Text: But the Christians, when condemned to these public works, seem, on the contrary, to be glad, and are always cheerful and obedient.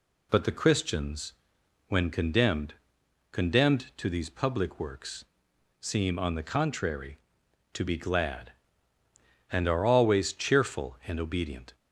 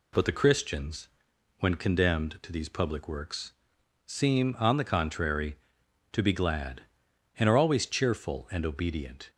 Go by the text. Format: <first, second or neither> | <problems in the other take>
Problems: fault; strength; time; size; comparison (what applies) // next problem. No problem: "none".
second | says "condemned" twice; at 3.3 s